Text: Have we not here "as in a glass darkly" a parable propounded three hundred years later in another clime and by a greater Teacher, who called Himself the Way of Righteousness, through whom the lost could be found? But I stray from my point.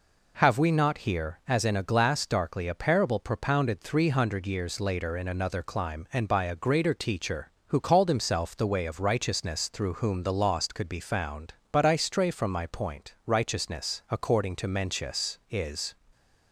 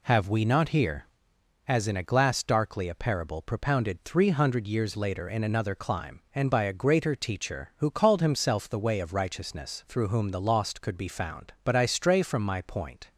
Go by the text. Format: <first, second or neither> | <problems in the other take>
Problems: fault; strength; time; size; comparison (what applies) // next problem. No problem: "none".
second | goes on to say "Righteousness according to Mencius is"; strong; from 13.2 s on; 2.7 s long